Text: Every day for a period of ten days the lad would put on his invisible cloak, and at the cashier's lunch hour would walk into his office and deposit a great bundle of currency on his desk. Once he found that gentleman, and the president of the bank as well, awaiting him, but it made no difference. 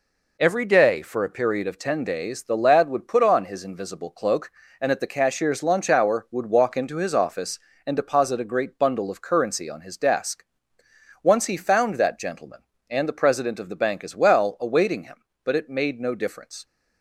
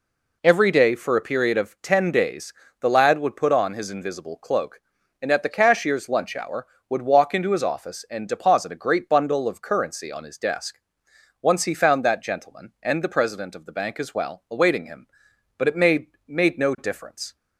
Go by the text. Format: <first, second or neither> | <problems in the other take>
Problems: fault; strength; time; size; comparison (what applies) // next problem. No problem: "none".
first | pauses between "days" and "the"; slight; at 2.5 s; 0.26 s long // says "made" twice; at 16.2 s